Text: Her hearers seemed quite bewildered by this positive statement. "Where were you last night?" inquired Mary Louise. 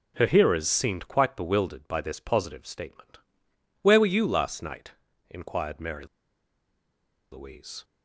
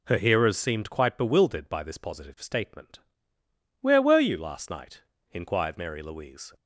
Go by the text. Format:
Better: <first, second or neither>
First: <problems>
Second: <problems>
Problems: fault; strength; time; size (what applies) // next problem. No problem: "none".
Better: second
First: pauses between "Mary" and "Louise"; strong; at 6.0 s; 1.2 s long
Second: none